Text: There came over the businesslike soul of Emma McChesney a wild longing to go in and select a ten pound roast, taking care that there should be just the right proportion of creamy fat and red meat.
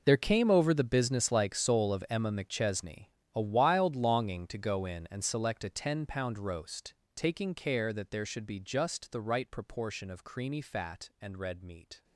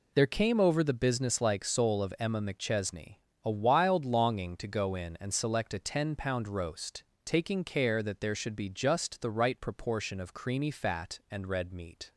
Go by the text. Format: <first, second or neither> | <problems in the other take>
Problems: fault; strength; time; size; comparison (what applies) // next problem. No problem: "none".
second | gets quieter; strong; throughout; 17 dB // pauses between "McChesney" and "a"; slight; at 3.0 s; 0.28 s long; slight in the second